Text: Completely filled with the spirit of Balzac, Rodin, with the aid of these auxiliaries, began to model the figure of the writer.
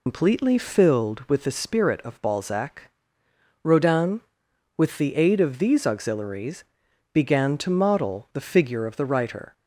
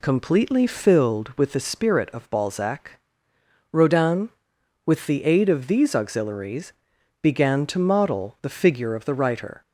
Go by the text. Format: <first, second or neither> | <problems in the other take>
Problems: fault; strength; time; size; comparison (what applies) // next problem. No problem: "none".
second | loses the start of "Completely"; at 0.0 s; 135 ms